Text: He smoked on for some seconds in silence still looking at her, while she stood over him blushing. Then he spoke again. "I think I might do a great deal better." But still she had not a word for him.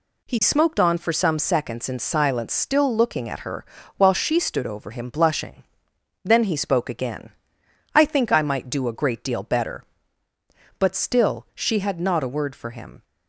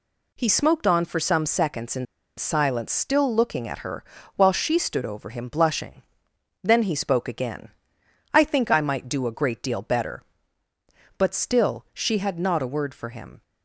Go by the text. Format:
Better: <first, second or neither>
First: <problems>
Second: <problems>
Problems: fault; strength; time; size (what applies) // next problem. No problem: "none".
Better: first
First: none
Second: pauses between "in" and "silence"; slight; at 2.0 s; 0.32 s long